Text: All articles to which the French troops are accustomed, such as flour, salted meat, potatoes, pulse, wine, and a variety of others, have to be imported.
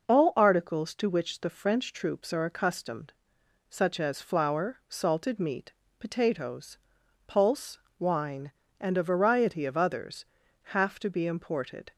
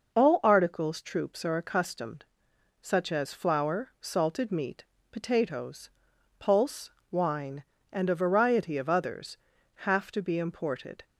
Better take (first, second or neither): first